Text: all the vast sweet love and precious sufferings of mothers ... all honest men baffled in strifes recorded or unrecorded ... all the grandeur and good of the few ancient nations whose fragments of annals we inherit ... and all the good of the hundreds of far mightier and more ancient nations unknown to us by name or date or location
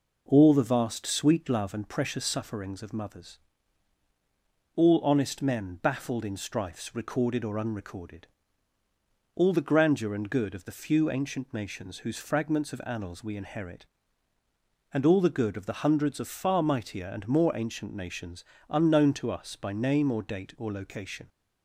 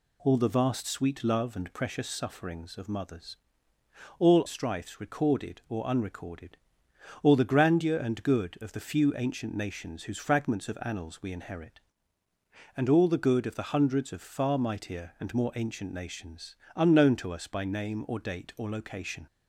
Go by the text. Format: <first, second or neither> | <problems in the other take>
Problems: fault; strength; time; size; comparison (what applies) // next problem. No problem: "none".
first | skips "honest men baffled in"; at 4.4 s // pauses between "nations" and "unknown"; slight; at 16.5 s; 0.18 s long; slight in the first